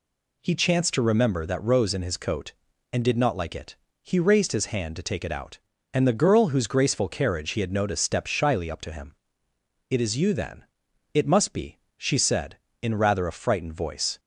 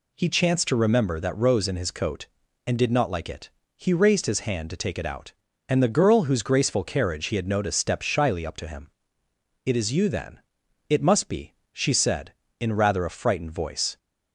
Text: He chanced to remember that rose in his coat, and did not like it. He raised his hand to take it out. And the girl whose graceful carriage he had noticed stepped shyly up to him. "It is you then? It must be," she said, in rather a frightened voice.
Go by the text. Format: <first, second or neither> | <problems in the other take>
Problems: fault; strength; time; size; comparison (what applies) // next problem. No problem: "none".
neither | none